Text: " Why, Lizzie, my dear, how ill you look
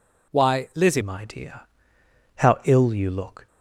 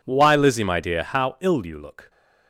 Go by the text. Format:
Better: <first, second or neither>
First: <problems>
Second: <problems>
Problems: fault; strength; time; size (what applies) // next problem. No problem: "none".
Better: second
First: changes voice at "my"; from 1.0 s on; 2.4 s long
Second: none